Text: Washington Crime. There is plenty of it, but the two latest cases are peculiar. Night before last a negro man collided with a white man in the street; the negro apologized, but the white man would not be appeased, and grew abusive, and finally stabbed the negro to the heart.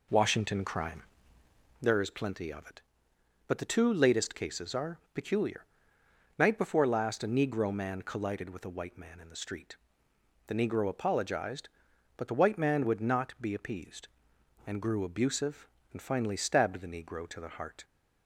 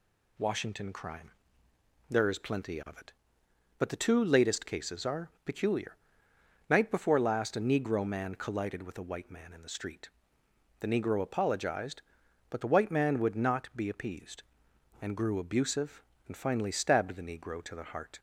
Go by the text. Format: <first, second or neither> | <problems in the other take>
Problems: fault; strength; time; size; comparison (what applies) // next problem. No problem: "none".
second | starts louder than the rest; noticeable; until 1.9 s; 4 dB